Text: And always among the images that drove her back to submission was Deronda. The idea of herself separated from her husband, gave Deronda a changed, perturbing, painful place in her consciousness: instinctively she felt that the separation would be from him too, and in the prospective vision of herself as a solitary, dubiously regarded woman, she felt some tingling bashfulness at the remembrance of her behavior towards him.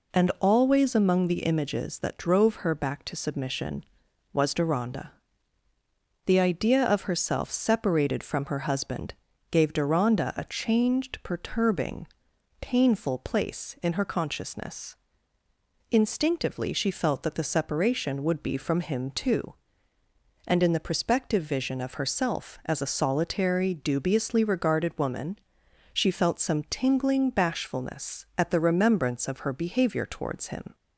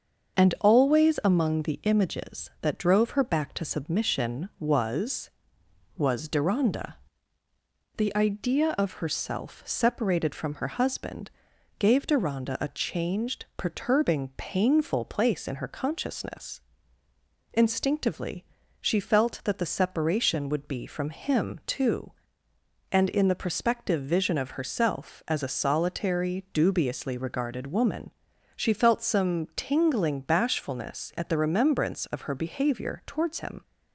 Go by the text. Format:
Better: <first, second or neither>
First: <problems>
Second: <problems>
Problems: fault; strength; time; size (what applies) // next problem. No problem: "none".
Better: first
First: none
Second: starts louder than the rest; until 1.4 s; 6.5 dB // says "was" twice; at 5.9 s // pauses between "instinctively" and "she"; at 18.4 s; 0.38 s long